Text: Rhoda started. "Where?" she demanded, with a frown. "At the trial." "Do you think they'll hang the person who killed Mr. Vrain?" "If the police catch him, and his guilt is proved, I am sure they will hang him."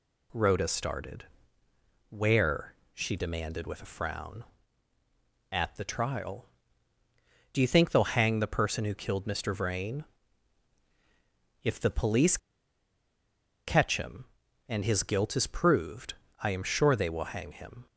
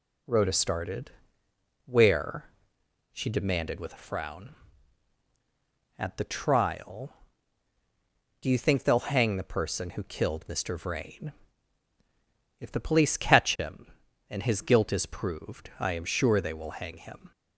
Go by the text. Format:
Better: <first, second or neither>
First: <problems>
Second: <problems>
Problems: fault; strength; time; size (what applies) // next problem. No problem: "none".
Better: second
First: pauses between "police" and "catch"; strong; at 12.3 s; 1.3 s long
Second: none